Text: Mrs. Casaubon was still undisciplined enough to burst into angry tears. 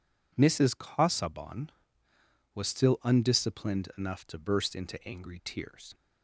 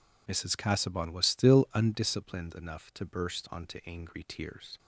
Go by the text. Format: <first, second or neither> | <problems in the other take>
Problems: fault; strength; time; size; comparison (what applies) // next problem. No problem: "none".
first | says "onto" for "into"; at 3.5 s